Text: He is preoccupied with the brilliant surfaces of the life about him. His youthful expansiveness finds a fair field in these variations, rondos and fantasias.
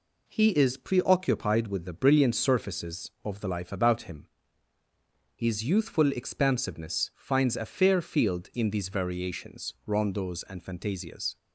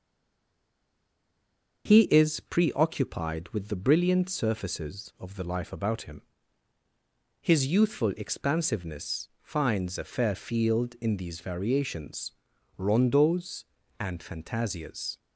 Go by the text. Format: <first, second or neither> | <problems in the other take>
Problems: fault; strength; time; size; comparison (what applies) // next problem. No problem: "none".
first | stays silent before the first word; noticeable; until 1.8 s; 1.8 s long // starts louder than the rest; until 2.8 s; 6.5 dB